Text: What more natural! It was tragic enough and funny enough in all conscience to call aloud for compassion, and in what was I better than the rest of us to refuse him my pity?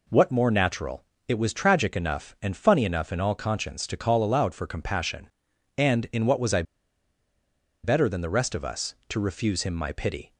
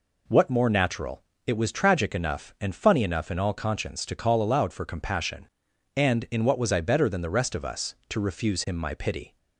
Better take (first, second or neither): second